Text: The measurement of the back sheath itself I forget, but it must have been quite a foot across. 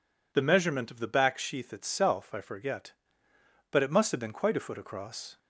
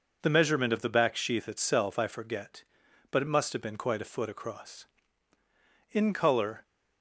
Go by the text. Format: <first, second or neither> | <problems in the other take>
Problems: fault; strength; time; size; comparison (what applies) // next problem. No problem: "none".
first | goes on to say "In colour"; noticeable; from 5.9 s on; 0.72 s long